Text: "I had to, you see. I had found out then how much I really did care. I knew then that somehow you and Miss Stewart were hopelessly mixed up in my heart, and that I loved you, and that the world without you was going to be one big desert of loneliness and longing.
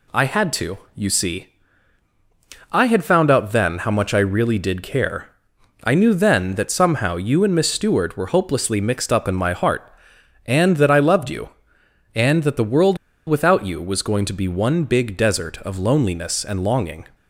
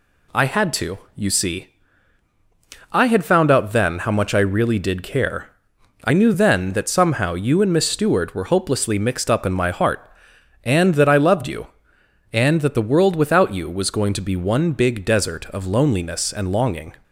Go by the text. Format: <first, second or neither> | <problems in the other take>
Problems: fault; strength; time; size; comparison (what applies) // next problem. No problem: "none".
second | pauses between "world" and "without"; slight; at 12.9 s; 0.29 s long